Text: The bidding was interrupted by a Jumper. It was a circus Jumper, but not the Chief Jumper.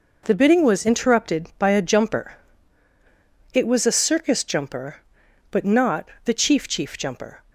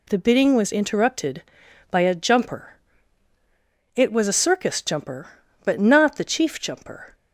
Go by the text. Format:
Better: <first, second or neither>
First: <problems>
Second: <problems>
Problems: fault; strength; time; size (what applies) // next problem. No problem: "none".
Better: second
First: pauses between "not" and "the"; slight; at 6.0 s; 0.16 s long // says "Chief" twice; at 6.6 s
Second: none